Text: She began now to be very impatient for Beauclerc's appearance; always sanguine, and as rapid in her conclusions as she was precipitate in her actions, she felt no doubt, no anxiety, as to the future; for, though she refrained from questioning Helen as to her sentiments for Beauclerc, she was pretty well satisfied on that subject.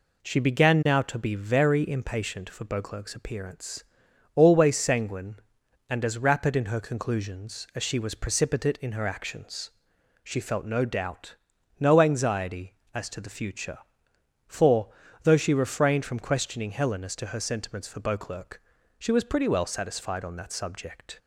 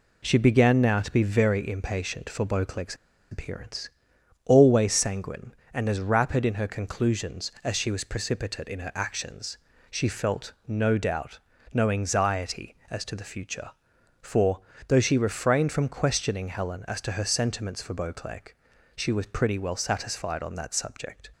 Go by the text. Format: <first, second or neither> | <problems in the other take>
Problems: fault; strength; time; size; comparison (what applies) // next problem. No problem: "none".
first | pauses between "Beauclerc's" and "appearance"; slight; at 2.9 s; 0.35 s long